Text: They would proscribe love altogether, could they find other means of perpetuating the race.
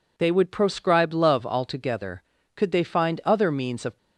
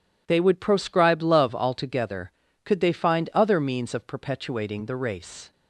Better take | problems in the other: second | stops before "perpetuating the race"; at 3.9 s

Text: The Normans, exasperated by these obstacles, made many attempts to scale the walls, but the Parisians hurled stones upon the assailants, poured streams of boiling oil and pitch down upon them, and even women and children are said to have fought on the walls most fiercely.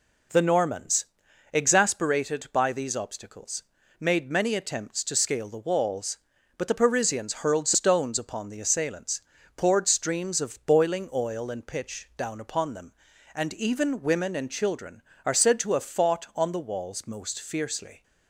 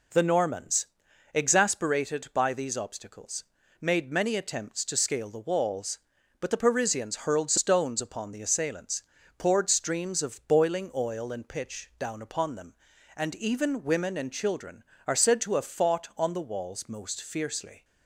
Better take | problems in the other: neither | none

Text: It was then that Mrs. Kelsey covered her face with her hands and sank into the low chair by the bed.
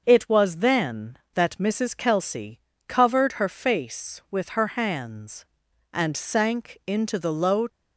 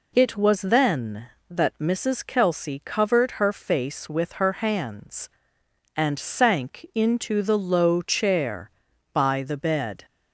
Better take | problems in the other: second | starts louder than the rest; until 1.0 s; 6 dB // pauses between "Kelsey" and "covered"; slight; at 2.5 s; 0.28 s long // stops before "chair by the bed"; at 7.6 s

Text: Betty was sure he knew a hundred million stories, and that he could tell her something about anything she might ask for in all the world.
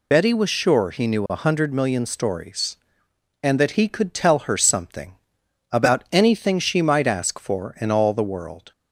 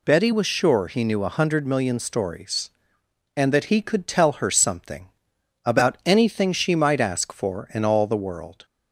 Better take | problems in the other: second | loses the start of "Betty"; at 0.1 s; 50 ms // pauses between "something" and "about"; noticeable; at 5.1 s; 0.56 s long; noticeable in the second

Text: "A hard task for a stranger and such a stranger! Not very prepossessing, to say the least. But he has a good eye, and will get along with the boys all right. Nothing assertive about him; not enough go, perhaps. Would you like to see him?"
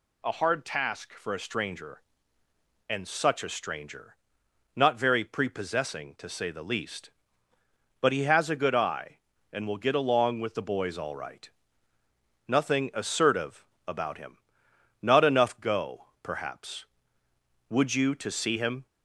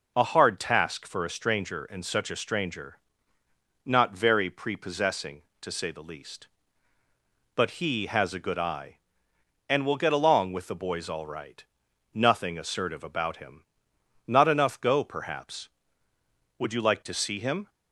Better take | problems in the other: second | pauses between "assertive" and "about"; slight; at 13.6 s; 0.20 s long // skips "like"; at 18.1 s

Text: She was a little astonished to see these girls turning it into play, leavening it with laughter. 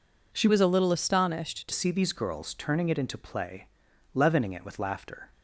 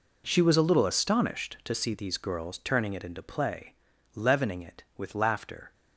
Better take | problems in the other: second | changes voice from "was" to "to"; from 0.4 to 1.7 s; 1.3 s long

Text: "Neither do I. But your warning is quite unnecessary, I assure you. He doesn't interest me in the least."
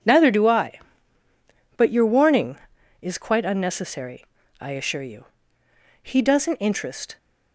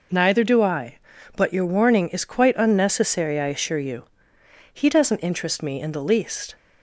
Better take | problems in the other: second | stops before "me in the least"; at 7.1 s

